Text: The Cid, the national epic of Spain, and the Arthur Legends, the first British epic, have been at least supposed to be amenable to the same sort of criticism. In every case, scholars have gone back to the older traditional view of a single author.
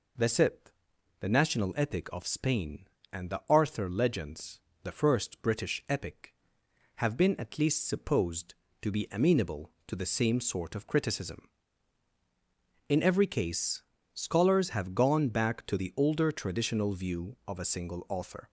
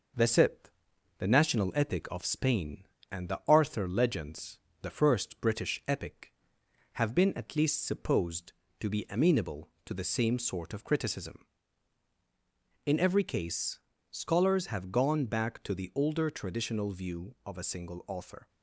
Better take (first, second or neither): first